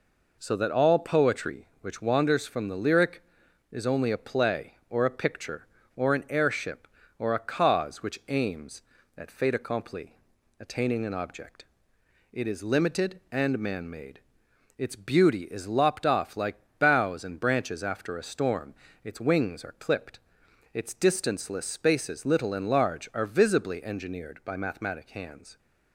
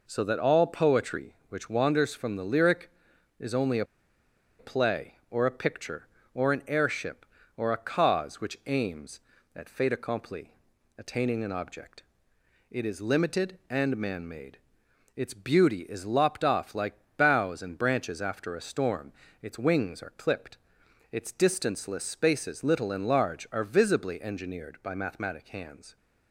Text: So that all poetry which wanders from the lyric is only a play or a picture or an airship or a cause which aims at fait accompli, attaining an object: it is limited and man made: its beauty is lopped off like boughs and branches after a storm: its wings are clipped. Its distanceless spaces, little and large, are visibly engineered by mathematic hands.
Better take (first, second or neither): first